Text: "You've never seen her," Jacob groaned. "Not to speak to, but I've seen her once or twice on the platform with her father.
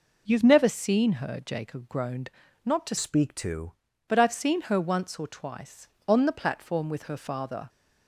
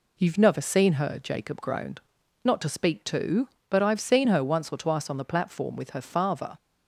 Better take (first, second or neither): second